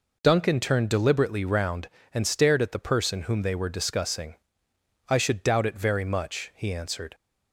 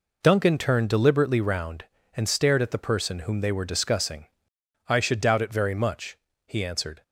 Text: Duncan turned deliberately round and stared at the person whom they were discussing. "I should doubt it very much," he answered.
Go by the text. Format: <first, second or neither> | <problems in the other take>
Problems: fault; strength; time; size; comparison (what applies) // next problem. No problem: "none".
neither | none